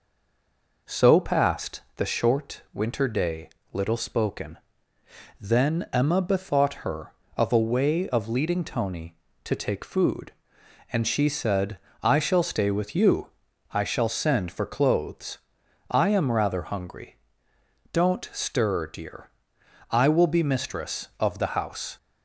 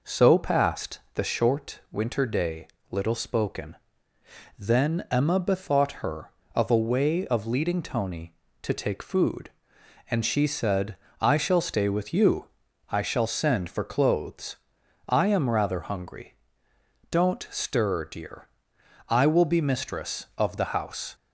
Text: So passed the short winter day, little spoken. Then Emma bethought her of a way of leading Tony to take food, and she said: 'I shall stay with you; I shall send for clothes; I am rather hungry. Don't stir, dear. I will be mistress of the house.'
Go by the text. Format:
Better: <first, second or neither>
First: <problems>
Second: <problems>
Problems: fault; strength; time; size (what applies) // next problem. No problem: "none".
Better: second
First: stays silent before the first word; slight; until 0.8 s; 0.8 s long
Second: none